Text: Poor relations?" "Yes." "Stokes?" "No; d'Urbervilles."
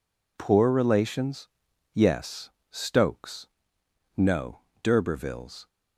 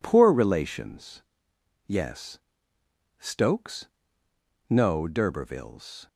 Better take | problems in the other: neither | none

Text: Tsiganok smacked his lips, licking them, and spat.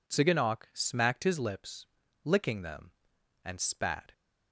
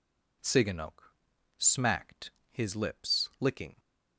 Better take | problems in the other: first | pauses between "Tsiganok" and "smacked"; noticeable; at 1.1 s; 0.46 s long // pauses between "smacked" and "his"; slight; at 2.2 s; 0.22 s long // stops before "them and spat"; at 3.7 s

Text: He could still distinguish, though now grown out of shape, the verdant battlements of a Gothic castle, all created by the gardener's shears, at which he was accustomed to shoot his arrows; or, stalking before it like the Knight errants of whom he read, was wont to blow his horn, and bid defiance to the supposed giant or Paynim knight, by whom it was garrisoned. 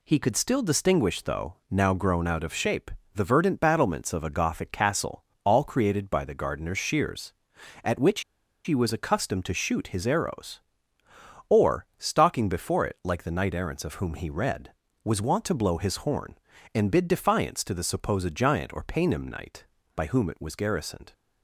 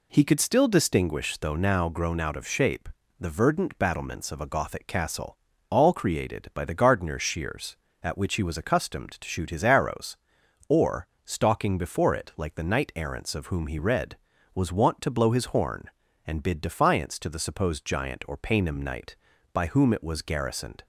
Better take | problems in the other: second | pauses between "which" and "he"; at 8.2 s; 0.43 s long

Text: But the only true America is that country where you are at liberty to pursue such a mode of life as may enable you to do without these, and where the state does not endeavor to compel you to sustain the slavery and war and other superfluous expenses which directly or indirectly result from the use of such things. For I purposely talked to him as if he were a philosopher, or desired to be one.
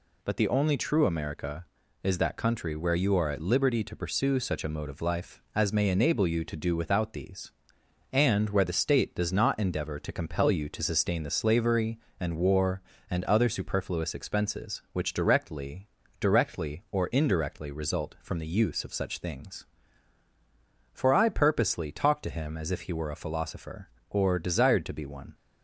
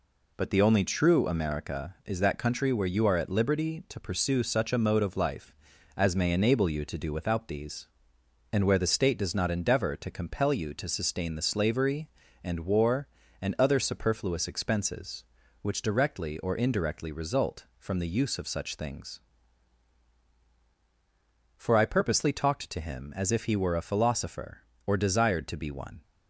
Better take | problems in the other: second | says "directly" twice; at 16.1 s

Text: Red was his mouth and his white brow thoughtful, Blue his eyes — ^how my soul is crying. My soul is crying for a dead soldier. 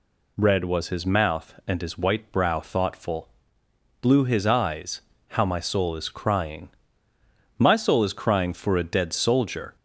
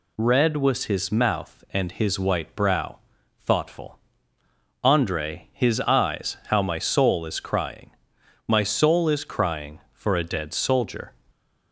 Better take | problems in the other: first | pauses between "brow" and "thoughtful"; noticeable; at 2.9 s; 0.46 s long // says "Andre" for "Blue"; at 4.8 s

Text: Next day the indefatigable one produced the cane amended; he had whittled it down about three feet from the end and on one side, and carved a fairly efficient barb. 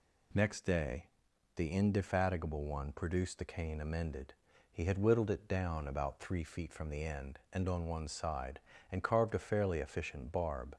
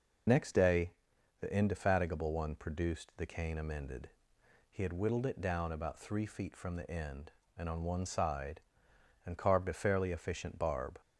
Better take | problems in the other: first | loses the start of "Next"; at 0.2 s; 25 ms // pauses between "day" and "the"; noticeable; at 0.9 s; 0.48 s long; noticeable in the first

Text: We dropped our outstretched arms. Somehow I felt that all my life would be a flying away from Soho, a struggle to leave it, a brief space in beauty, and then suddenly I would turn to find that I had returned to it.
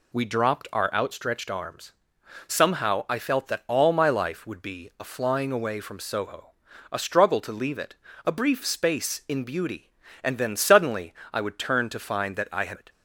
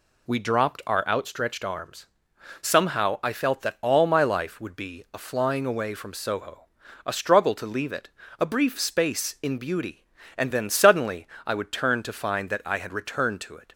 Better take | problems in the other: second | pauses between "suddenly" and "I"; slight; at 11.1 s; 0.18 s long; slight in the second // skips "returned to"; at 12.7 s

